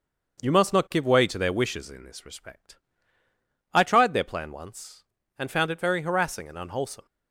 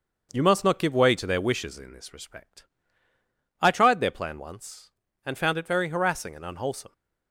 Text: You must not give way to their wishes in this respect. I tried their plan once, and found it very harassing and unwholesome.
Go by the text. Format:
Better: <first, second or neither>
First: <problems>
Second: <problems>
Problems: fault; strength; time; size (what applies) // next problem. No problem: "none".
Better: neither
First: starts louder than the rest; until 1.4 s; 6.5 dB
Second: starts louder than the rest; until 1.3 s; 6.5 dB